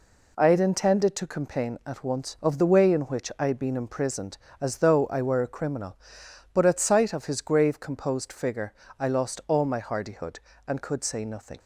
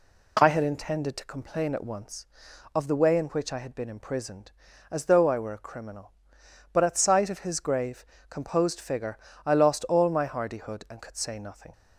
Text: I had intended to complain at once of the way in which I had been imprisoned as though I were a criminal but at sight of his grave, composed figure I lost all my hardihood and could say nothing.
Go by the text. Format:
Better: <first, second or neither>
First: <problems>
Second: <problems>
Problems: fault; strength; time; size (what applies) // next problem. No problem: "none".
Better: neither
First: pauses between "figure" and "I"; slight; at 8.7 s; 0.24 s long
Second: pauses between "figure" and "I"; slight; at 9.1 s; 0.26 s long